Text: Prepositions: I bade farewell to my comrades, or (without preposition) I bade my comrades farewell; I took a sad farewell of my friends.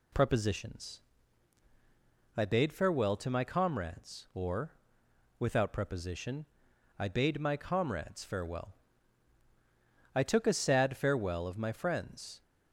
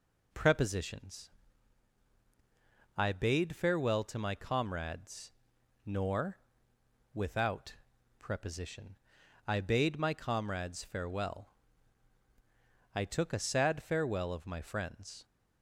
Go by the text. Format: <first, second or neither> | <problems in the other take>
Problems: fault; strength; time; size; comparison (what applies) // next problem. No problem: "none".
first | says "nor" for "or"; at 5.8 s // pauses between "without" and "preposition"; at 7.7 s; 0.42 s long